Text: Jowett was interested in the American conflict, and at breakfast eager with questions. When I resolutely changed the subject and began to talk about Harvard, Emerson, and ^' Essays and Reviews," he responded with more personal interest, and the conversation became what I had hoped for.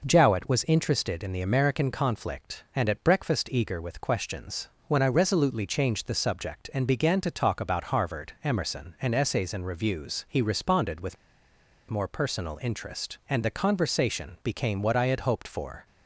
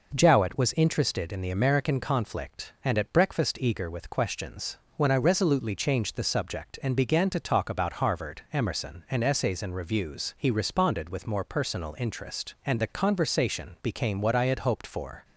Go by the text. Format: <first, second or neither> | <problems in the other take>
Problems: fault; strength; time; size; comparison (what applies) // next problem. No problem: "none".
second | pauses between "with" and "more"; noticeable; at 11.1 s; 0.75 s long